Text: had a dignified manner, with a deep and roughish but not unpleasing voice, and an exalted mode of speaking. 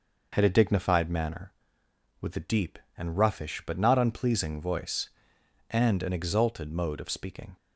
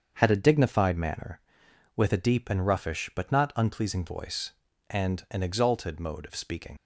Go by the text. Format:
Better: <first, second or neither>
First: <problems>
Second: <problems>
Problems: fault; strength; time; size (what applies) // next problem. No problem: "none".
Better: first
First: none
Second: starts louder than the rest; strong; until 1.1 s; 7 dB // leaves "speaking" unfinished; at 6.7 s; 60 ms